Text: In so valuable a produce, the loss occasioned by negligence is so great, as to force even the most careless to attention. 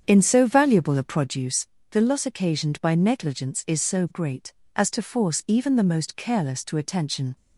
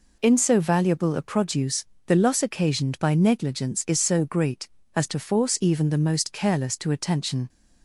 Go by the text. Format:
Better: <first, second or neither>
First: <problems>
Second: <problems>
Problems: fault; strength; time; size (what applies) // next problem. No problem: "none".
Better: second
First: starts louder than the rest; strong; until 1.3 s; 8 dB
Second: none